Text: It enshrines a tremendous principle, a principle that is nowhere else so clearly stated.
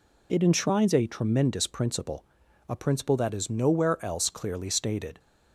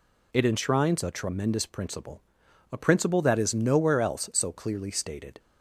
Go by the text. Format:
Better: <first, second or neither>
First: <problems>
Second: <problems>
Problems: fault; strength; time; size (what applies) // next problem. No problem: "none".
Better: second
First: skips "so"; at 4.2 s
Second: none